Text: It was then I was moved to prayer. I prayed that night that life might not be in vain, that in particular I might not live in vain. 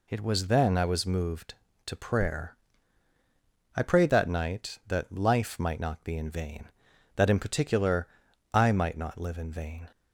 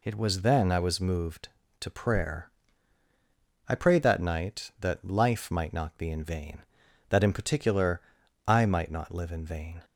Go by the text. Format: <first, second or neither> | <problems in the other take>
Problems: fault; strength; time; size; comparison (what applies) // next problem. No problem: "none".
neither | pauses between "particular" and "I"; the same in both